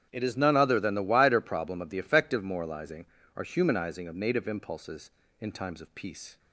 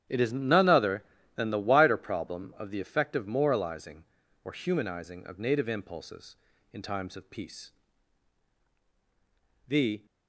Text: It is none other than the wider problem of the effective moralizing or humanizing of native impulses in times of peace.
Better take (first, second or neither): first